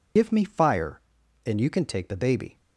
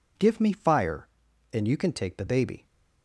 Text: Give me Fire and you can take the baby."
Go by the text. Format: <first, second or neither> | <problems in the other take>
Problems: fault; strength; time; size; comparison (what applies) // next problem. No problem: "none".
second | loses the start of "Give"; at 0.1 s; 65 ms